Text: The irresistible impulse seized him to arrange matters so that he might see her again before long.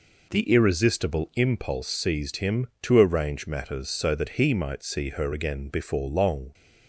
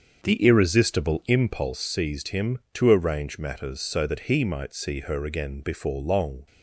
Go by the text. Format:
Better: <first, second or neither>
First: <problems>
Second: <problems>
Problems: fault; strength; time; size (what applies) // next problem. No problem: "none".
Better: first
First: none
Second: starts louder than the rest; until 1.8 s; 6.5 dB